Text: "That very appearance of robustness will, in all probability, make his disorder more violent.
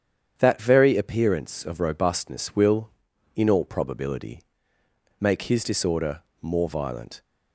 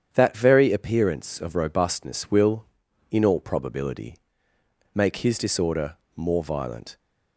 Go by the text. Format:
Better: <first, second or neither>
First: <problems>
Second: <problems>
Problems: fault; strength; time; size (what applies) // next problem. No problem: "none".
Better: neither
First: starts louder than the rest; strong; until 1.3 s; 8.5 dB // pauses between "disorder" and "more"; slight; at 6.2 s; 0.20 s long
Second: starts louder than the rest; strong; until 1.1 s; 8.5 dB // pauses between "disorder" and "more"; slight; at 5.9 s; 0.20 s long